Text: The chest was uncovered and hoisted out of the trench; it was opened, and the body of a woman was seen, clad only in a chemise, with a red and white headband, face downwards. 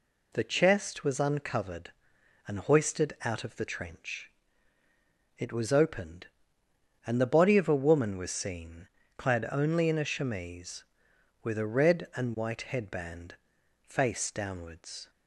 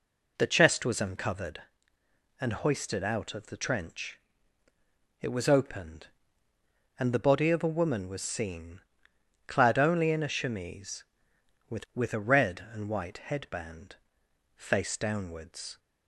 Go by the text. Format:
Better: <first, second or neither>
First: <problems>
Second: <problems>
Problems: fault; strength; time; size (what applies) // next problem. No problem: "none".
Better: first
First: none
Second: says "with" twice; at 11.9 s